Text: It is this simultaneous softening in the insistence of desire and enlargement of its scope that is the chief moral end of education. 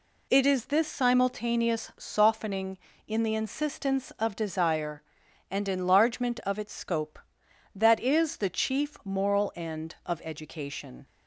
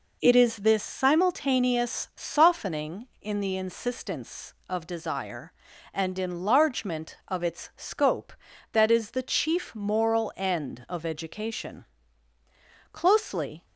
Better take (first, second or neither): first